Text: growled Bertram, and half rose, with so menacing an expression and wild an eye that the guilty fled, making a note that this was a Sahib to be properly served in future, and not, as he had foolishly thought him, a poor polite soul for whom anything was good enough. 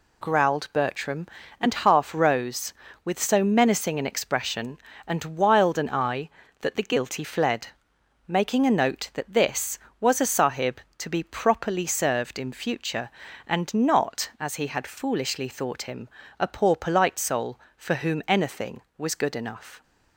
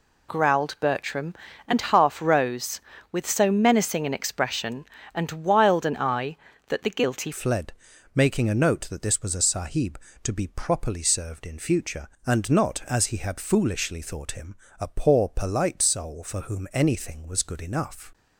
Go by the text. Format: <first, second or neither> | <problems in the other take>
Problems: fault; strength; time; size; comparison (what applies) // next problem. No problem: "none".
first | changes voice at "fled"; from 7.3 s on; 10.8 s long